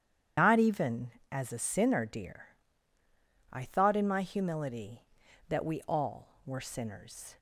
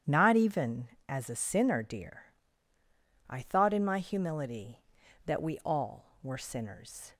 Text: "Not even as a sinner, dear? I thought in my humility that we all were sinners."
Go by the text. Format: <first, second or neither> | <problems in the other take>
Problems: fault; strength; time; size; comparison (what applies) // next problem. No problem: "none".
second | loses the start of "Not"; at 0.3 s; 85 ms // starts louder than the rest; strong; until 1.6 s; 9.5 dB; strong in the second